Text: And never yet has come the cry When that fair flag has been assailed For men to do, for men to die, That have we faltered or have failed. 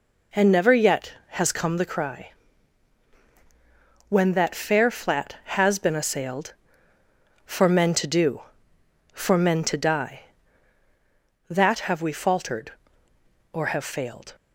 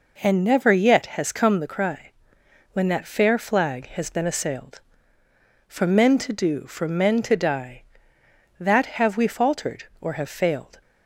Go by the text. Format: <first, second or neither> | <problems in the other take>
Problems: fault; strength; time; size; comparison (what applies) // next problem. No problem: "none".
second | pauses between "cry" and "When"; strong; at 2.3 s; 1.7 s long; noticeable in the second // says "flat" for "flag"; at 4.8 s